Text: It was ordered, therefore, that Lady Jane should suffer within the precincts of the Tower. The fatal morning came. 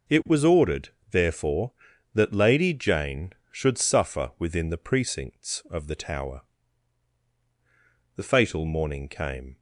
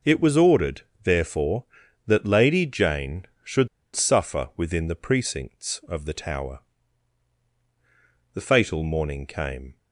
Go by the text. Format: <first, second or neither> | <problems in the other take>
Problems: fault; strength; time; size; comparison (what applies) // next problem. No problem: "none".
first | pauses between "should" and "suffer"; slight; at 3.6 s; 0.27 s long